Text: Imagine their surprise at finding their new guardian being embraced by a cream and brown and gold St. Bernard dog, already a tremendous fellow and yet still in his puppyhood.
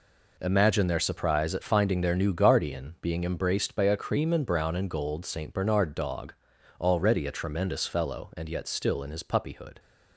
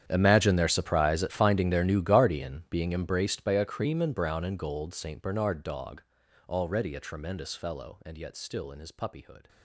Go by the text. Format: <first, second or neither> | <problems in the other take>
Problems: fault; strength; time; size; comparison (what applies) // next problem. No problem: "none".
first | gets quieter; strong; throughout; 19 dB